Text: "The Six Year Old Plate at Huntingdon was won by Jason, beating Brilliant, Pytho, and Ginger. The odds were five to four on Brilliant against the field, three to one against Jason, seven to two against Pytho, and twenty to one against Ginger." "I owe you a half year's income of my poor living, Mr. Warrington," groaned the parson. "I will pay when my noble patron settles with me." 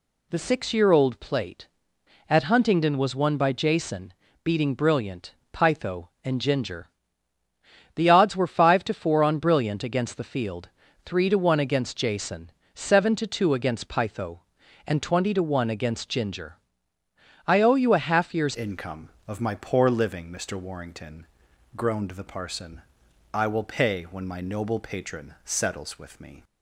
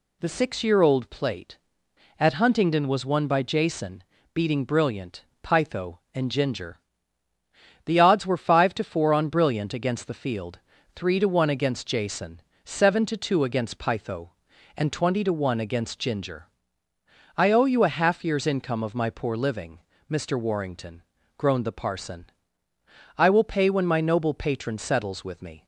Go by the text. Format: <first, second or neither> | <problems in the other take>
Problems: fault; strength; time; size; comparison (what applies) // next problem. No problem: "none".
second | changes voice at "income"; from 18.5 s on; 7.9 s long